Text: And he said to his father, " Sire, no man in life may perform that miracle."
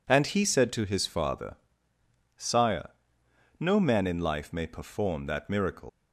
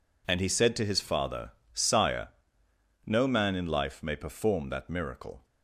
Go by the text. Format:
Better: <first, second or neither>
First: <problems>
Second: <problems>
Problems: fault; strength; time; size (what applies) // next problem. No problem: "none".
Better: second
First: leaves "miracle" unfinished; at 5.8 s; 125 ms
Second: none